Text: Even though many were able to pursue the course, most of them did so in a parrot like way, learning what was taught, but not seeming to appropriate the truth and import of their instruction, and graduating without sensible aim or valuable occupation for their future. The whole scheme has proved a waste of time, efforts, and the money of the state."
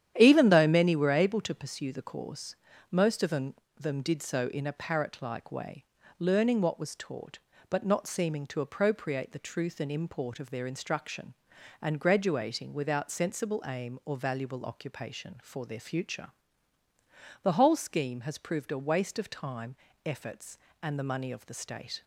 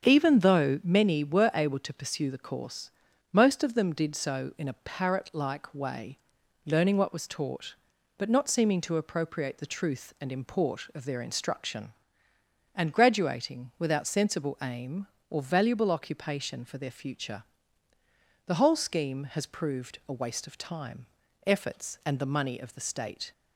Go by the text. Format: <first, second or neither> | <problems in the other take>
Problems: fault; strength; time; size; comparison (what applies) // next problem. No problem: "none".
second | starts louder than the rest; strong; until 1.2 s; 10.5 dB; strong in the second // says "them" twice; at 3.7 s